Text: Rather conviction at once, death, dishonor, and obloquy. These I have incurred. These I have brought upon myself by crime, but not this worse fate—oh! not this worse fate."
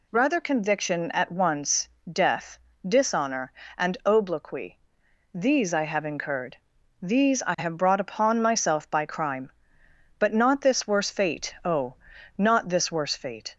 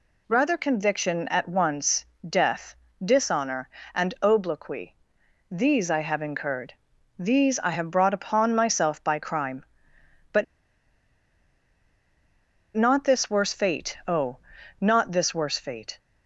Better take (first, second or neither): first